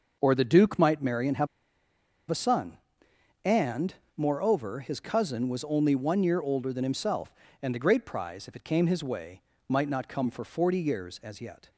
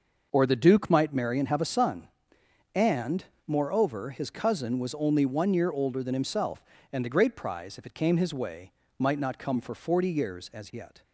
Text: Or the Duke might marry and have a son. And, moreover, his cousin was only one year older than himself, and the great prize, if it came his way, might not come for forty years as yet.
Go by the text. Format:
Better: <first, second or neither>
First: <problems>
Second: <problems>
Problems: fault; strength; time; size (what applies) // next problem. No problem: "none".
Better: second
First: pauses between "have" and "a"; noticeable; at 1.4 s; 0.83 s long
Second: none